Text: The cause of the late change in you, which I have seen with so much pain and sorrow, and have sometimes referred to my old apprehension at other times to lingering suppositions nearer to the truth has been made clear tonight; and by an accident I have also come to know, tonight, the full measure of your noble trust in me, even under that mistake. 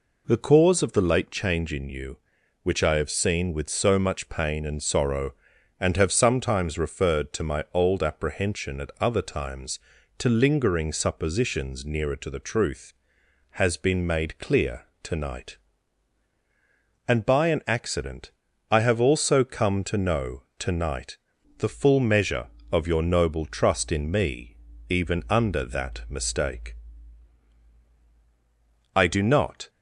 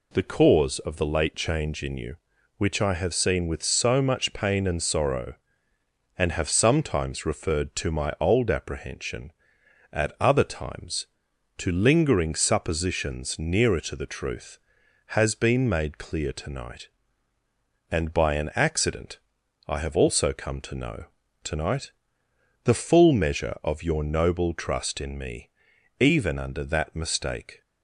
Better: second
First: pauses between "clear" and "tonight"; slight; at 14.8 s; 0.18 s long // pauses between "accident" and "I"; at 18.3 s; 0.40 s long // goes on to say "I do not"; noticeable; from 28.9 s on; 0.74 s long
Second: pauses between "accident" and "I"; noticeable; at 19.1 s; 0.46 s long

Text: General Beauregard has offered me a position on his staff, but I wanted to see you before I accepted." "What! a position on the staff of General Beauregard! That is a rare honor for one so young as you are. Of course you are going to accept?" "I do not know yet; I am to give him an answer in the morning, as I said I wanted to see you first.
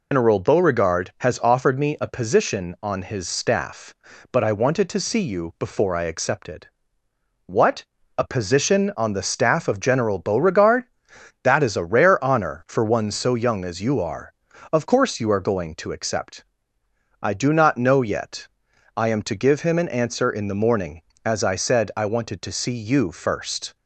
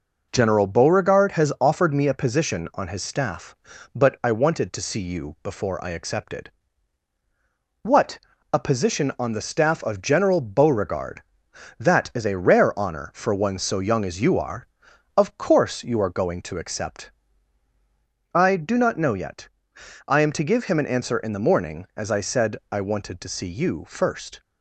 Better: second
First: loses the start of "General"; at 0.1 s; 145 ms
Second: none

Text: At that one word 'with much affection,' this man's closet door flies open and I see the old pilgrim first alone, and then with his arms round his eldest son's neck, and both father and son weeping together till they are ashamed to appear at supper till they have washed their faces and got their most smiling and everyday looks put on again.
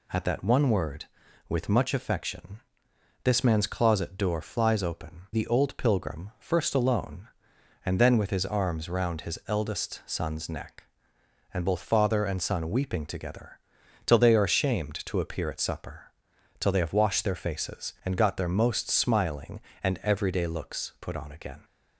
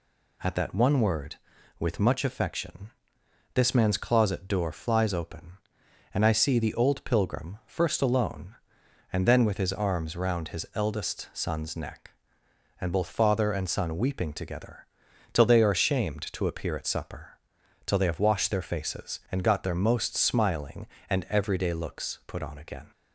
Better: second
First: skips "and I see"; at 5.2 s // pauses between "together" and "till"; noticeable; at 13.5 s; 0.48 s long // pauses between "supper" and "till"; noticeable; at 16.0 s; 0.50 s long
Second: pauses between "together" and "till"; noticeable; at 14.8 s; 0.48 s long // pauses between "supper" and "till"; noticeable; at 17.3 s; 0.50 s long

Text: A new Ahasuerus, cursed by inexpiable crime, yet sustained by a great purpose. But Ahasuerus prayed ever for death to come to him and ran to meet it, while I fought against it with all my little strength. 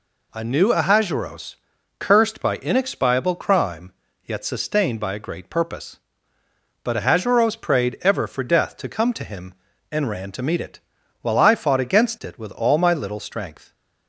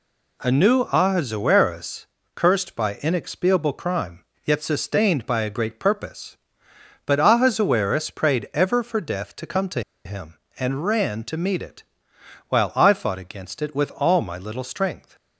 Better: first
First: none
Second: pauses between "to" and "him"; slight; at 9.8 s; 0.23 s long

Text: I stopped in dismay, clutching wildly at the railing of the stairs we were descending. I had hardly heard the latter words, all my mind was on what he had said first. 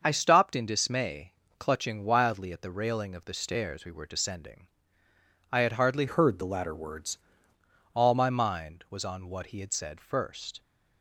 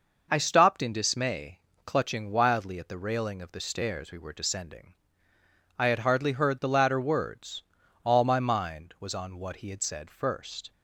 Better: second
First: starts louder than the rest; until 1.0 s; 6.5 dB // changes voice from "heard" to "words"; from 6.0 to 7.1 s; 1.1 s long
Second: none

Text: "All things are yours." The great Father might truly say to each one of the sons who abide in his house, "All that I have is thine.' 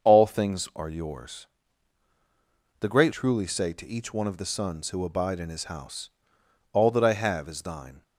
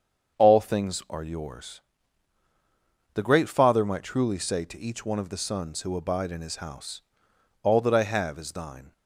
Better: second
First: starts louder than the rest; until 1.1 s; 6.5 dB // skips "Father might"; at 3.1 s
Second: starts louder than the rest; until 1.4 s; 7 dB

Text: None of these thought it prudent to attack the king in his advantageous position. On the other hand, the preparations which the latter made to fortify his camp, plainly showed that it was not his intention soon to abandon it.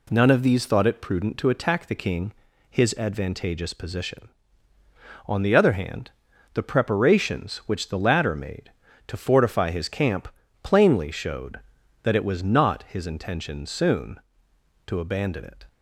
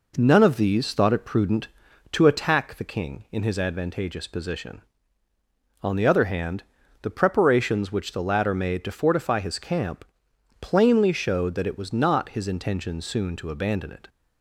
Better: second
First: skips "in"; at 2.5 s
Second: none

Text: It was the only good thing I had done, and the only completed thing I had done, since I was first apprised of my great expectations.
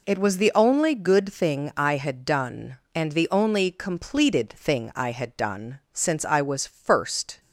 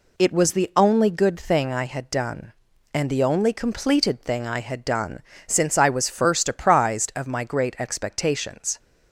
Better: second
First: stops before "apprised of my great expectations"; at 7.3 s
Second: none

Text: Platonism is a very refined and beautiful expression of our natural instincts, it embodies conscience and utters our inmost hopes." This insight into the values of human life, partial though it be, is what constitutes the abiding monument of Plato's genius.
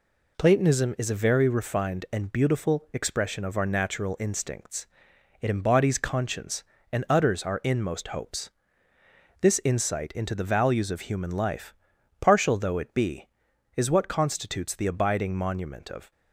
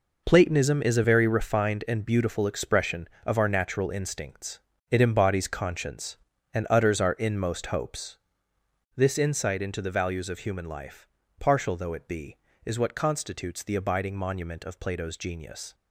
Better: second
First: stops before "Plato's genius"; at 16.1 s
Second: none

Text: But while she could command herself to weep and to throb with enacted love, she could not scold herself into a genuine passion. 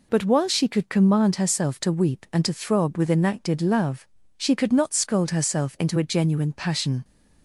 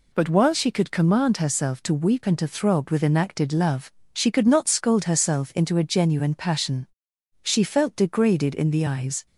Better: first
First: none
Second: goes on to say "She felt degraded in the eyes"; strong; from 7.4 s on; 1.8 s long

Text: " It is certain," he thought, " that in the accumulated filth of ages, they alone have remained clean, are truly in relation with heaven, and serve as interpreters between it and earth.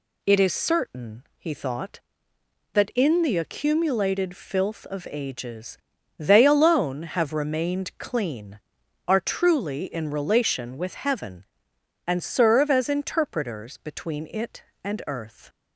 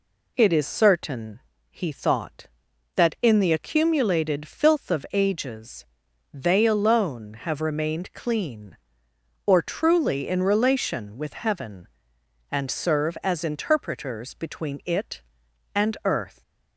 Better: first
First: none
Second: says "or" for "are"; at 9.4 s

